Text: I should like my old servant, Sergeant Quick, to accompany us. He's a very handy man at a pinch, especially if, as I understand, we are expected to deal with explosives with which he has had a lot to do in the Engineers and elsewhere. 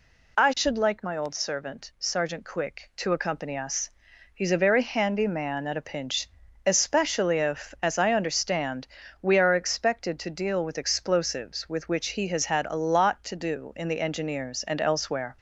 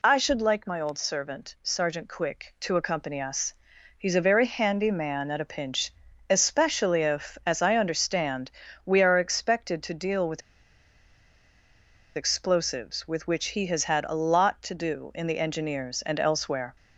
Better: first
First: none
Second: pauses between "with" and "explosives"; strong; at 10.4 s; 1.7 s long

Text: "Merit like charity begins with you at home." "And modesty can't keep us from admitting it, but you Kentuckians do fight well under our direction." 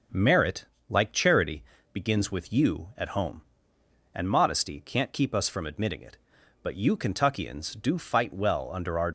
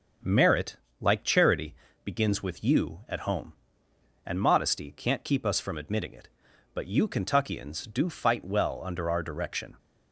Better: second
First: starts louder than the rest; until 1.3 s; 6.5 dB // pauses between "Merit" and "like"; slight; at 0.6 s; 0.24 s long // pauses between "charity" and "begins"; slight; at 1.6 s; 0.30 s long // stops before "direction"; at 9.0 s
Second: starts louder than the rest; until 1.4 s; 6.5 dB // pauses between "Merit" and "like"; slight; at 0.7 s; 0.24 s long // pauses between "charity" and "begins"; slight; at 1.7 s; 0.30 s long

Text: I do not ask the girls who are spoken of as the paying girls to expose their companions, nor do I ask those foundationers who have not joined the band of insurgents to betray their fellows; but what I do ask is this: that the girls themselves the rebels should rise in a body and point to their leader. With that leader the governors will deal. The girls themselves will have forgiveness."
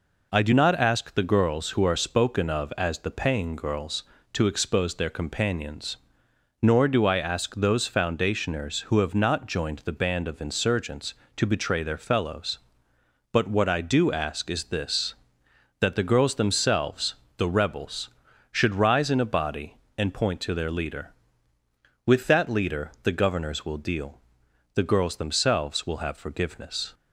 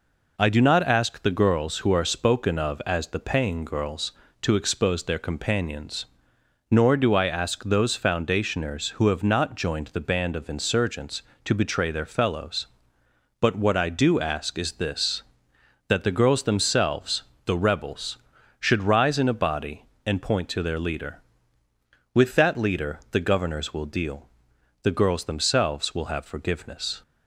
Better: neither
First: pauses between "themselves" and "the"; slight; at 17.1 s; 0.20 s long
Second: pauses between "themselves" and "the"; slight; at 17.2 s; 0.20 s long

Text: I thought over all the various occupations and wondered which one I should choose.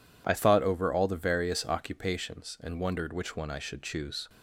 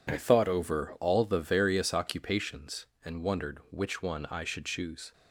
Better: neither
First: none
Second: none

